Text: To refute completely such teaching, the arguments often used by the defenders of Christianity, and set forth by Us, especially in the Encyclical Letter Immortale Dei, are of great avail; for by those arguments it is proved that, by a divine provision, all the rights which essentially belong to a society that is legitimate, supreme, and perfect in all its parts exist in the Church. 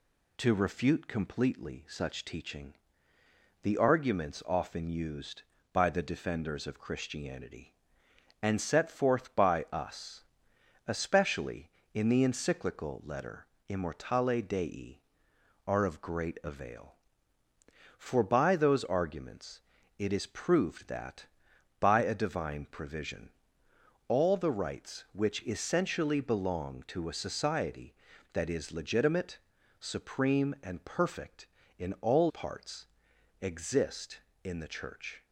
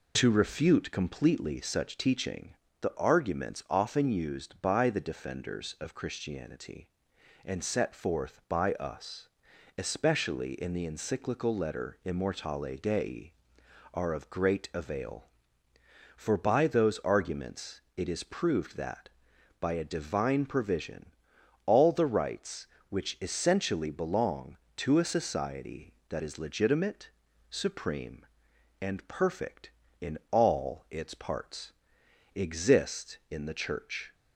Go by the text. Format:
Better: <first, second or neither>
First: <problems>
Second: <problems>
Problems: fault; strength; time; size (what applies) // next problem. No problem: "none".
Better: second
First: pauses between "Letter" and "Immortale"; slight; at 13.4 s; 0.22 s long // pauses between "arguments" and "it"; at 19.6 s; 0.38 s long // skips "its"; at 32.2 s // pauses between "parts" and "exist"; noticeable; at 32.8 s; 0.56 s long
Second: pauses between "arguments" and "it"; slight; at 17.8 s; 0.16 s long // pauses between "parts" and "exist"; noticeable; at 31.7 s; 0.62 s long